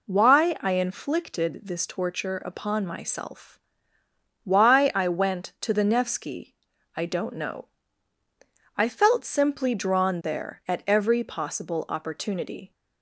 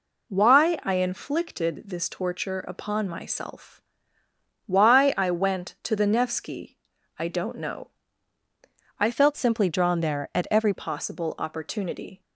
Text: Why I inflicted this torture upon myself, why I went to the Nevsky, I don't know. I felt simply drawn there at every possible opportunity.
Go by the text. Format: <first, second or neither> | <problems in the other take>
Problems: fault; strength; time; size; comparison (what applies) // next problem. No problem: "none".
first | changes voice from "felt" to "every"; from 9.1 to 10.7 s; 1.6 s long